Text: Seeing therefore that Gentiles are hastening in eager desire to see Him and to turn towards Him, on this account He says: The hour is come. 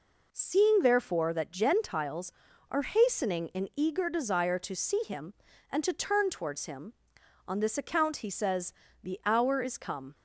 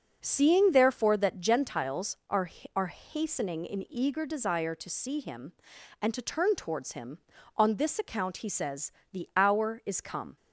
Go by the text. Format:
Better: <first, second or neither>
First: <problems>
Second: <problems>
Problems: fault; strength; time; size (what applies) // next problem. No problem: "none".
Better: first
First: none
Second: says "are" twice; at 2.7 s